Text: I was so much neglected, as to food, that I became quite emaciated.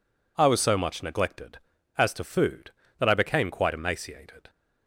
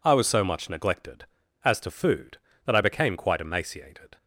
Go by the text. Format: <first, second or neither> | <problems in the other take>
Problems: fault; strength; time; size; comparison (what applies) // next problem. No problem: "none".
neither | none